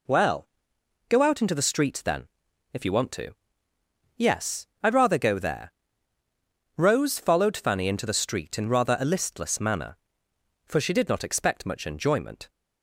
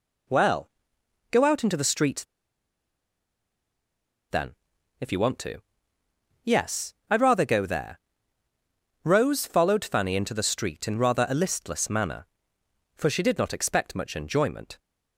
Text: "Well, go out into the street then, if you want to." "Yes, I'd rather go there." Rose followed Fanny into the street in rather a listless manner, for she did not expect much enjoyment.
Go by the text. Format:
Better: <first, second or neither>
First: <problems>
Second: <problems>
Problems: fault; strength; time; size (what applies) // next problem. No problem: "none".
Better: first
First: none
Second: pauses between "street" and "then"; strong; at 2.2 s; 2.0 s long